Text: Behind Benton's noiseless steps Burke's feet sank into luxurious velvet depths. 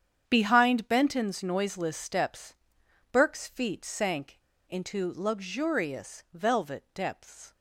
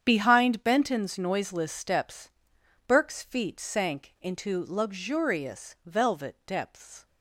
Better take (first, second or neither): second